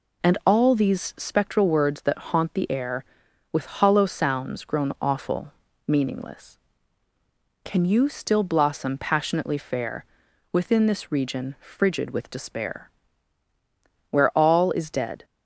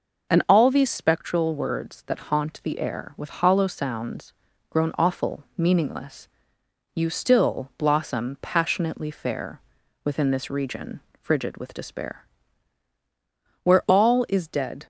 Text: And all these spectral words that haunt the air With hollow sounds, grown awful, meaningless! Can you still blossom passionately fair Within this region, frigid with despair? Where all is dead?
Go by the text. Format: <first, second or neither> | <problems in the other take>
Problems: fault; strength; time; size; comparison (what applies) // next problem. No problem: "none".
first | skips "Can"; at 6.6 s // pauses between "fair" and "Within"; at 9.6 s; 0.44 s long; noticeable in the first